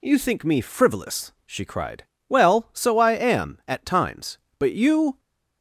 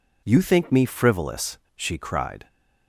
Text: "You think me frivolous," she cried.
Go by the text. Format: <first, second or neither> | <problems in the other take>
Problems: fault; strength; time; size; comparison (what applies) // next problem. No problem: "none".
second | goes on to say "Well so I am at times But you"; strong; from 2.2 s on; 2.9 s long